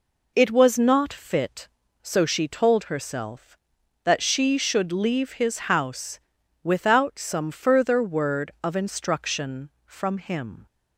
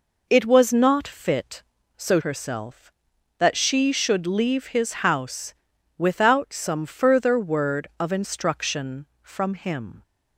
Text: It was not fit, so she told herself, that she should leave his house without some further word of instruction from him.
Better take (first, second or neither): first